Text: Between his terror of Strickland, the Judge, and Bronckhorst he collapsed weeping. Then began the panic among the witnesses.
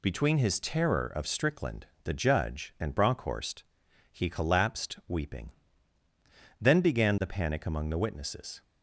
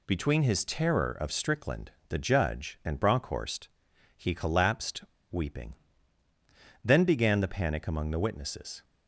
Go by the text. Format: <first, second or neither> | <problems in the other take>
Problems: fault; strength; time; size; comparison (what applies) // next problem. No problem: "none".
first | pauses between "Bronckhorst" and "he"; noticeable; at 3.6 s; 0.46 s long; noticeable in the first // pauses between "collapsed" and "weeping"; slight; at 5.0 s; 0.26 s long